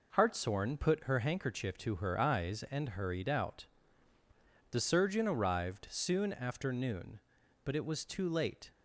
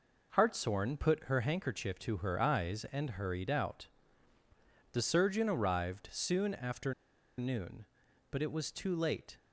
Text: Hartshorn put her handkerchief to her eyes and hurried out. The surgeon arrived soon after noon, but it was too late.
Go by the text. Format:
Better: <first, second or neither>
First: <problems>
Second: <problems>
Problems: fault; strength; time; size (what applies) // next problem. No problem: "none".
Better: first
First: none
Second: pauses between "after" and "noon"; at 6.9 s; 0.44 s long